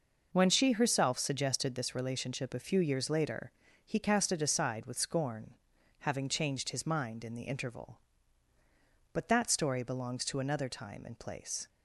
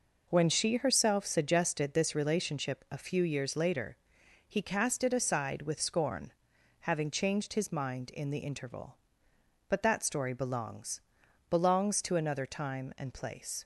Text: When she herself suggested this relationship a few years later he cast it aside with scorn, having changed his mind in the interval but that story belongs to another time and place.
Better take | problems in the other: first | pauses between "later" and "he"; noticeable; at 3.9 s; 0.54 s long; slight in the first // says "belongs" twice; at 11.4 s

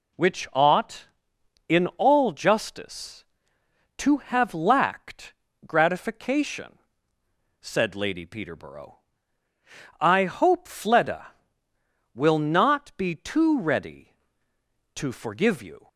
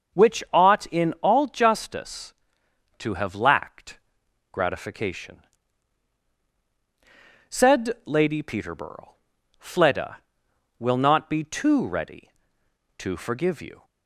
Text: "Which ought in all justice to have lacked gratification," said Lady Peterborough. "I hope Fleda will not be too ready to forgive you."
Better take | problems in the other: first | starts louder than the rest; until 1.3 s; 6.5 dB // pauses between "lacked" and "gratification"; noticeable; at 3.9 s; 0.56 s long; slight in the first // skips "I hope"; at 9.3 s

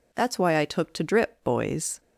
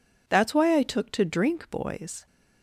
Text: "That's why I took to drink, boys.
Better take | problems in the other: second | says "drip" for "drink"; at 1.0 s

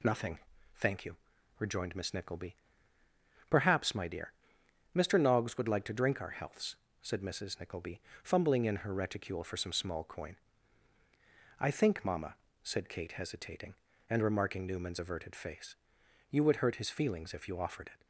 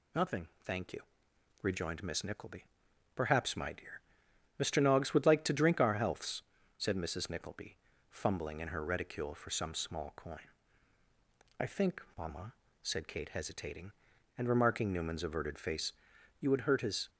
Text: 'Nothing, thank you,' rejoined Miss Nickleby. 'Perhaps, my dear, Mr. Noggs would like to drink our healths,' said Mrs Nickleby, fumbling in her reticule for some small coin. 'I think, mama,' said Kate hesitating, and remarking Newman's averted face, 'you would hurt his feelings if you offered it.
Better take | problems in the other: first | stops before "feelings if you offered it"; at 17.0 s

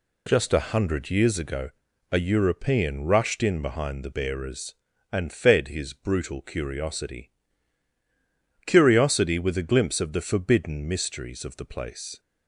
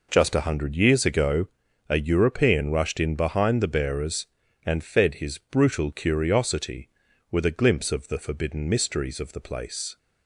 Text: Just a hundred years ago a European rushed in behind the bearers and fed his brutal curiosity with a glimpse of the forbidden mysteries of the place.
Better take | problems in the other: second | pauses between "ago" and "a"; at 1.6 s; 0.42 s long; also in the second // says "curiosity" twice; at 8.6 s

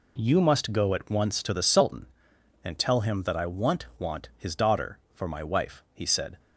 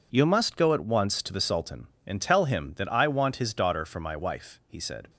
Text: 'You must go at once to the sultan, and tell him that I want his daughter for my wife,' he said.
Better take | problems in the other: second | says "want" twice; at 3.9 s

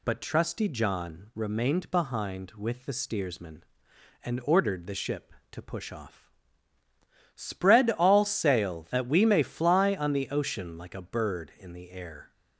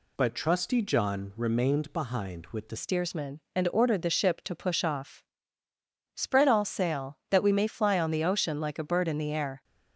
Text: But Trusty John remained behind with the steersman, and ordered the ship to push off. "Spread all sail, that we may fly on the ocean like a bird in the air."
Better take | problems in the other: first | changes voice at "steersman"; from 2.7 s on; 6.9 s long

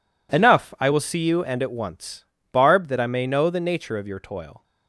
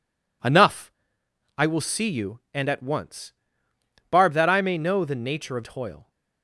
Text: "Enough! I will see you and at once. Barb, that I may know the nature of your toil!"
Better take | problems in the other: first | skips "your"; at 5.6 s

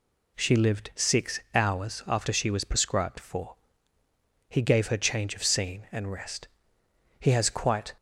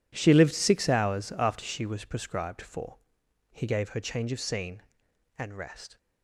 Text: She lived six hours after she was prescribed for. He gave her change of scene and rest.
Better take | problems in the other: second | goes on to say "He has quite"; noticeable; from 7.1 s on; 0.76 s long

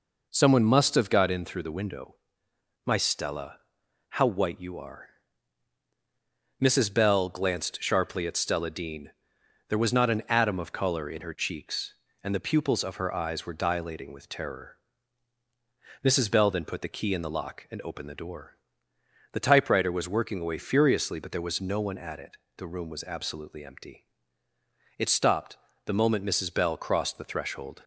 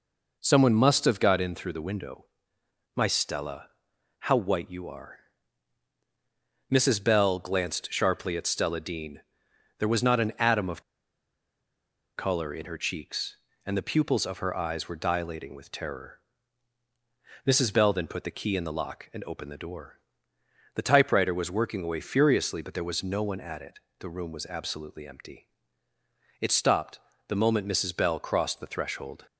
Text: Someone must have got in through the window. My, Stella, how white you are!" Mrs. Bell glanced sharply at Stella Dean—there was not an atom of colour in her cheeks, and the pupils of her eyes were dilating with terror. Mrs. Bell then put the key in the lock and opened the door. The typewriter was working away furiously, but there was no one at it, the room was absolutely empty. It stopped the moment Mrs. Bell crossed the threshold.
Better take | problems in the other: first | pauses between "of" and "colour"; strong; at 10.8 s; 1.3 s long // pauses between "stopped" and "the"; slight; at 26.9 s; 0.30 s long; slight in the first

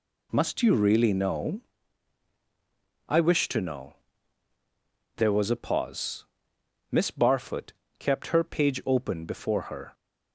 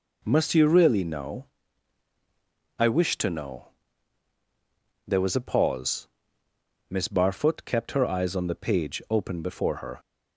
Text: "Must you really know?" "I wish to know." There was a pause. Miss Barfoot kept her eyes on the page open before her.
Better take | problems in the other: second | pauses between "Barfoot" and "kept"; slight; at 7.7 s; 0.26 s long // skips "eyes on the"; at 8.4 s

